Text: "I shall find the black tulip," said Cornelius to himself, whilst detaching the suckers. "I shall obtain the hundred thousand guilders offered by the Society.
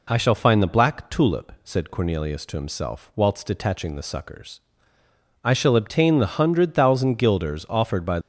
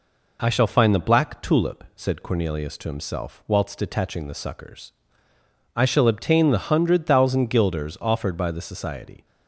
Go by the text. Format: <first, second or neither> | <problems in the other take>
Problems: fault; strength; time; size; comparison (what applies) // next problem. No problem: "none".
second | stops before "the Society"; at 8.2 s